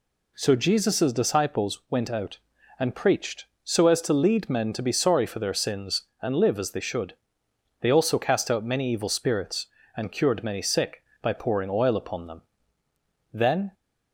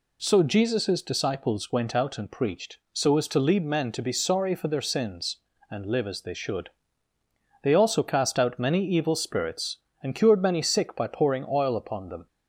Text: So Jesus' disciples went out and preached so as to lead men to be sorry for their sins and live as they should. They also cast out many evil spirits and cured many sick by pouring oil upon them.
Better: second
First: goes on to say "Then"; slight; from 13.3 s on; 0.42 s long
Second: none

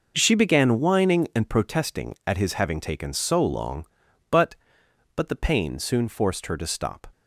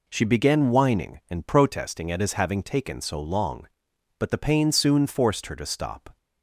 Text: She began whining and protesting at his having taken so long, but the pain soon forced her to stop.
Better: second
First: says "but" twice; at 5.1 s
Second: none

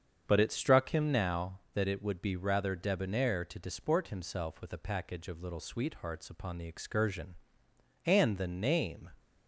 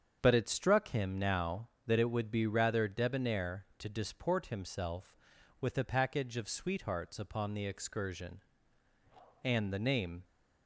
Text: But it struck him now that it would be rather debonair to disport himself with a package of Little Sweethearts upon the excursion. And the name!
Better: first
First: starts louder than the rest; strong; until 1.2 s; 7.5 dB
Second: starts louder than the rest; strong; until 1.2 s; 7 dB // skips "Little"; at 6.4 s

